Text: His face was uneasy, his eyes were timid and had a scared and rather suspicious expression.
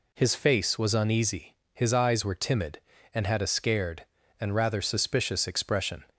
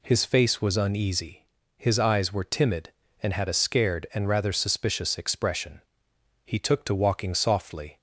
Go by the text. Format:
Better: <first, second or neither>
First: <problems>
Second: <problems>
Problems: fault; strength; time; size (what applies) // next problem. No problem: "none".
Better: first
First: none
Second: goes on to say "He took to walking softly"; from 6.4 s on; 1.5 s long